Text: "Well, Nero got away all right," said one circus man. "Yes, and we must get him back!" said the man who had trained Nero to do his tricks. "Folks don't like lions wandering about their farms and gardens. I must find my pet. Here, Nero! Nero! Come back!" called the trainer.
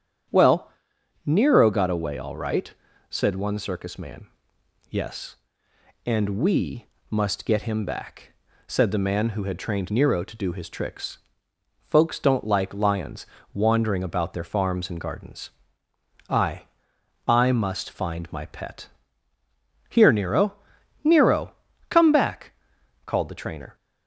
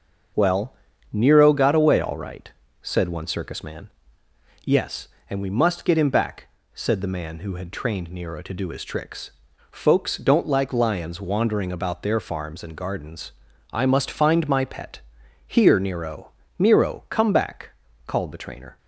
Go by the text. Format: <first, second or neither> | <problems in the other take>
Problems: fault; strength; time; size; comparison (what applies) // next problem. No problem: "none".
second | starts louder than the rest; strong; until 1.8 s; 9 dB; also in the second // pauses between "we" and "must"; slight; at 6.8 s; 0.24 s long // pauses between "lions" and "wandering"; slight; at 13.2 s; 0.30 s long // says "I" twice; at 17.2 s